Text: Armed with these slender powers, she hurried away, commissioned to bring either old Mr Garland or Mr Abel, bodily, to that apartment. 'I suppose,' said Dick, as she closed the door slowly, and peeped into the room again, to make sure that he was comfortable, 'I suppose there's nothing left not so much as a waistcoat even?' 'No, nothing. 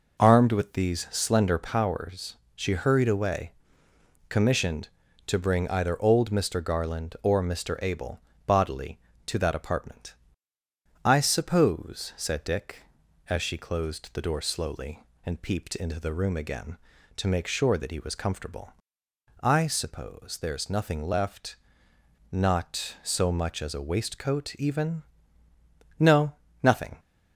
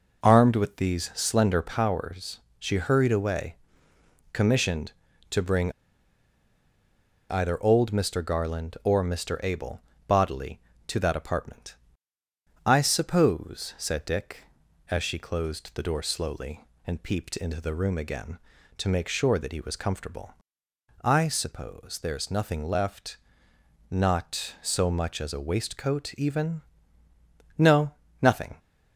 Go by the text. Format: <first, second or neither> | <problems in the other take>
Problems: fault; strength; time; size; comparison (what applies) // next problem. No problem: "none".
first | pauses between "bring" and "either"; strong; at 5.7 s; 1.5 s long // pauses between "left" and "not"; noticeable; at 23.1 s; 0.74 s long; noticeable in the first